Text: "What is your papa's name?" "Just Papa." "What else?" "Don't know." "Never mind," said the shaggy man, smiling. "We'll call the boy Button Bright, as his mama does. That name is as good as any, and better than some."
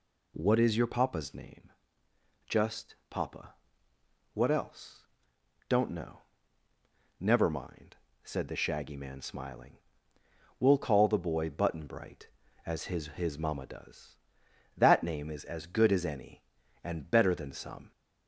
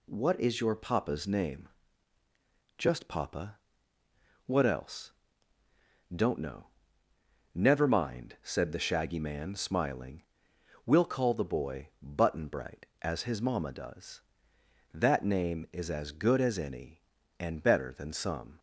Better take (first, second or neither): second